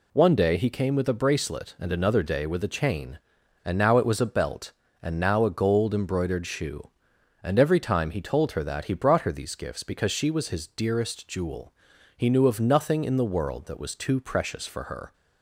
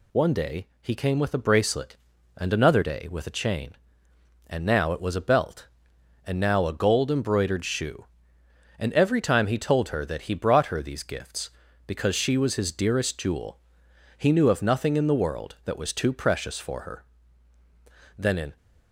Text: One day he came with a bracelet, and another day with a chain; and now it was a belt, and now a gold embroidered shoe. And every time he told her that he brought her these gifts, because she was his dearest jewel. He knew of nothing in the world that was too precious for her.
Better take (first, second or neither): first